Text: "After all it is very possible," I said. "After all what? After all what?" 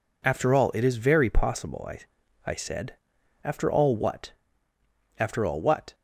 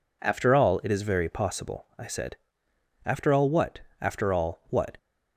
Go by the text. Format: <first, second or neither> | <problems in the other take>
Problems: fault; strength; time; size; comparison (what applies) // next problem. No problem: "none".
second | says "I" twice; at 2.4 s